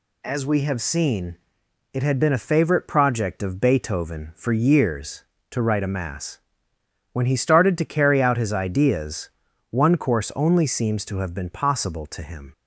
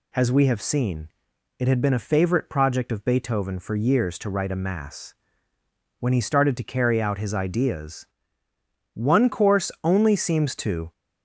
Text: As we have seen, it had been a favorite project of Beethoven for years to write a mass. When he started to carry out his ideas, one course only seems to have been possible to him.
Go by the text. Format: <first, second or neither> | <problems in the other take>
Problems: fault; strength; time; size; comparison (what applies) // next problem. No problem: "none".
first | stops before "have been possible to him"; at 10.9 s